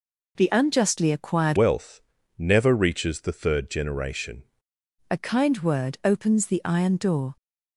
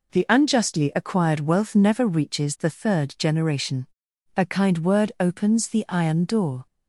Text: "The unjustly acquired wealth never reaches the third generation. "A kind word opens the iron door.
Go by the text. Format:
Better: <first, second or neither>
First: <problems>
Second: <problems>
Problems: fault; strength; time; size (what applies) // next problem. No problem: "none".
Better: second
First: changes voice from "wealth" to "generation"; from 1.5 to 4.4 s; 2.9 s long // pauses between "wealth" and "never"; slight; at 2.0 s; 0.36 s long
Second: none